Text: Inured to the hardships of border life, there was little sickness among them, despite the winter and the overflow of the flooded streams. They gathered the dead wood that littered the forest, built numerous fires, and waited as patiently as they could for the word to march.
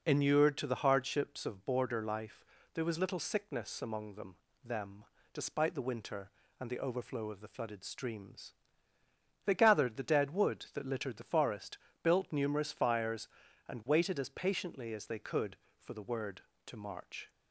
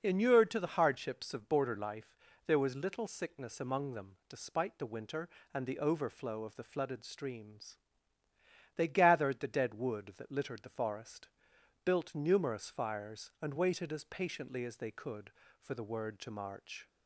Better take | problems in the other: second | says "them" twice; at 4.6 s

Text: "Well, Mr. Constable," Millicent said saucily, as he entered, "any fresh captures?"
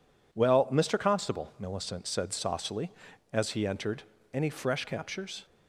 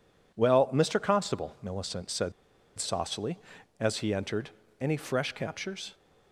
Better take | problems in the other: first | pauses between "said" and "saucily"; noticeable; at 2.3 s; 0.46 s long

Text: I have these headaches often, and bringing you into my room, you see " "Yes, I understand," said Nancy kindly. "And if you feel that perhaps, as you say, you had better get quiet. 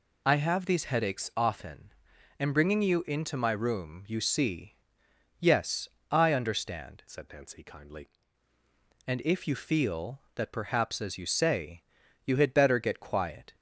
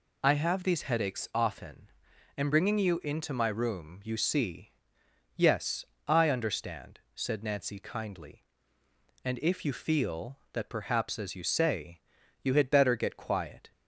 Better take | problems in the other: second | changes voice from "said" to "kindly"; from 7.0 to 8.0 s; 1.0 s long

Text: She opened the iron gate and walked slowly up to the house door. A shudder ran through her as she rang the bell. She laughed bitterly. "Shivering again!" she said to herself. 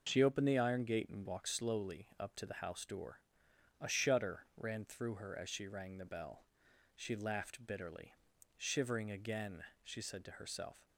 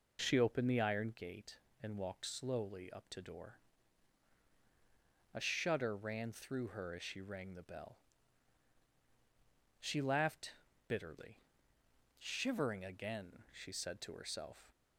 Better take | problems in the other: first | skips "the house"; at 3.2 s // pauses between "laughed" and "bitterly"; slight; at 10.5 s; 0.36 s long

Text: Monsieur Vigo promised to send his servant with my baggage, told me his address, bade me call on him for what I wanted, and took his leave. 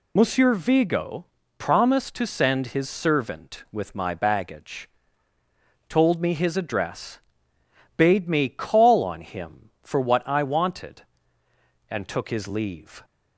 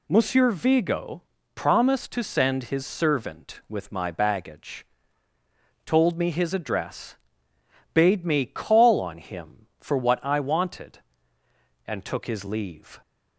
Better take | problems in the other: second | loses the start of "Monsieur"; at 0.1 s; 30 ms // pauses between "Vigo" and "promised"; slight; at 1.2 s; 0.32 s long; slight in the second

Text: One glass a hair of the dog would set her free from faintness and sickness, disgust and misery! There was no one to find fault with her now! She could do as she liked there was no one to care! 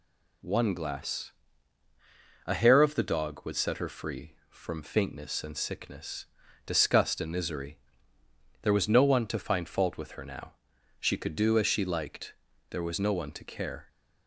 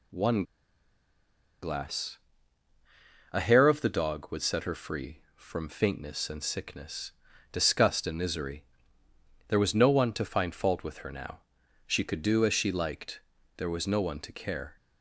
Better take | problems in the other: first | pauses between "One" and "glass"; at 0.4 s; 1.1 s long // pauses between "glass" and "a"; at 2.1 s; 1.1 s long; also in the first // pauses between "liked" and "there"; slight; at 13.2 s; 0.34 s long; slight in the first

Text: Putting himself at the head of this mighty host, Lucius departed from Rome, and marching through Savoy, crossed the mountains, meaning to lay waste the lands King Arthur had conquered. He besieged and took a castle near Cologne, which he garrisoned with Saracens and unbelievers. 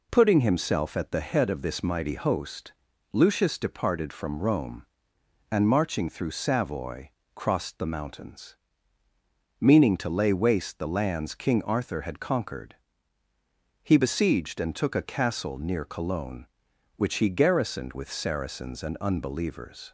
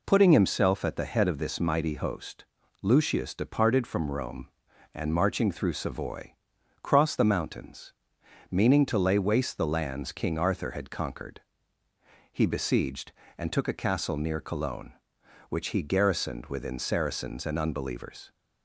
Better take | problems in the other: first | says "within" for "with"; at 16.4 s

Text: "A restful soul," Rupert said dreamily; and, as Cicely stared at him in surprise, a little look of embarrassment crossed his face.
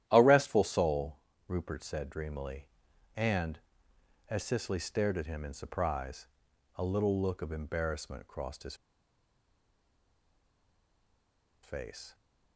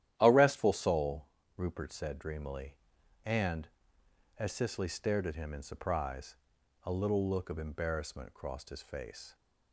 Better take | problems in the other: second | starts louder than the rest; strong; until 1.0 s; 12 dB; strong in the second // pauses between "his" and "face"; strong; at 8.7 s; 2.8 s long

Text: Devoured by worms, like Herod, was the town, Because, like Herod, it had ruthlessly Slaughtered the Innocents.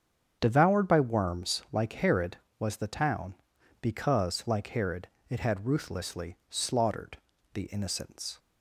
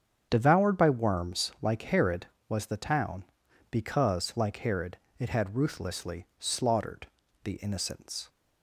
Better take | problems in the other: neither | starts louder than the rest; strong; the same in both // pauses between "ruthlessly" and "Slaughtered"; slight; the same in both // pauses between "Slaughtered" and "the"; the same in both

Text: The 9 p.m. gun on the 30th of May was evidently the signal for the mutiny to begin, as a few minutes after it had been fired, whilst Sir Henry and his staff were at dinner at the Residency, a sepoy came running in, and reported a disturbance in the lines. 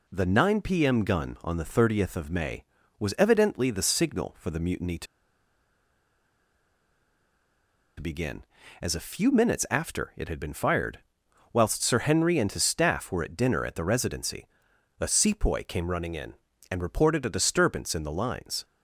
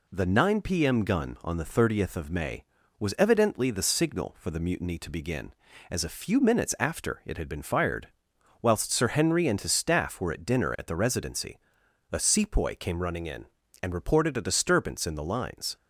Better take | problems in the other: second | pauses between "to" and "begin"; strong; at 5.0 s; 2.9 s long

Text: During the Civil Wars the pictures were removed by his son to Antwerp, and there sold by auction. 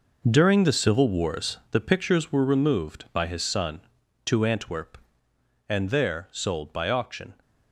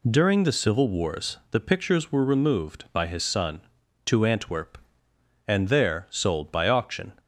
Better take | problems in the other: second | gets quieter; strong; throughout; 10 dB

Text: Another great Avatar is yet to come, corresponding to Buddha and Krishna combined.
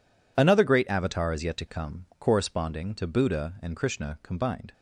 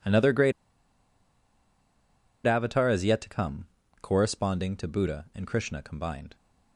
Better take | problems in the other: first | pauses between "great" and "Avatar"; strong; at 0.5 s; 1.9 s long

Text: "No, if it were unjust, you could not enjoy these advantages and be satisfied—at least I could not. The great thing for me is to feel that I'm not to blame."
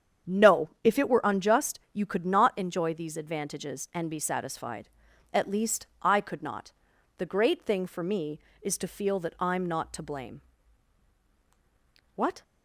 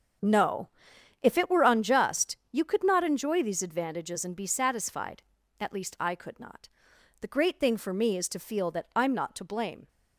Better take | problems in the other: second | starts louder than the rest; strong; until 1.4 s; 8 dB; strong in the second // goes on to say "What"; slight; from 12.1 s on; 0.28 s long

